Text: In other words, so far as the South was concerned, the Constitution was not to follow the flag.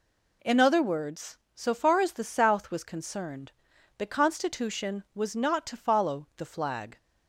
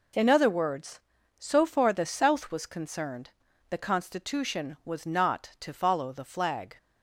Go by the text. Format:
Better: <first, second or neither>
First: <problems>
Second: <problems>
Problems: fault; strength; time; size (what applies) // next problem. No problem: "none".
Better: first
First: none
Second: skips "as"; at 1.9 s